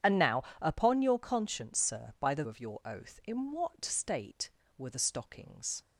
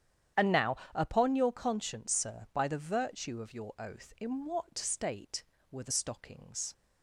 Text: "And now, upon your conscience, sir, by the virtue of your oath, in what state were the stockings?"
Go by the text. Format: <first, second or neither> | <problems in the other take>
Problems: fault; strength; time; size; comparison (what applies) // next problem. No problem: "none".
second | starts louder than the rest; strong; until 1.2 s; 9 dB; strong in the second // skips "virtue"; at 2.4 s